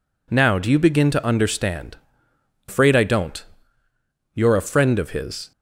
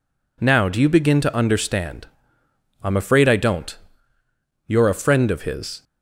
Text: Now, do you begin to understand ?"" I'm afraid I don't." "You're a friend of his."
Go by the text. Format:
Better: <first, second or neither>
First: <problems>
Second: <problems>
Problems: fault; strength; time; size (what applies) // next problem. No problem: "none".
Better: second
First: skips "I'm"; at 2.6 s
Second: none